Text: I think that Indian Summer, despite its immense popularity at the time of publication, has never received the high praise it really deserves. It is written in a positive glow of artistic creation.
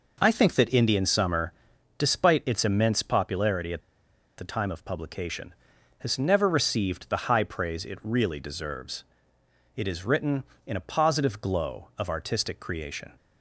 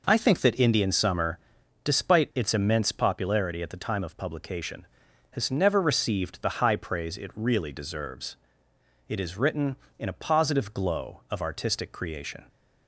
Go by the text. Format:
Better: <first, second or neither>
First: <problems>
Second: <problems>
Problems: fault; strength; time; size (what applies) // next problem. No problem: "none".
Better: second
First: pauses between "at" and "the"; noticeable; at 3.7 s; 0.59 s long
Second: none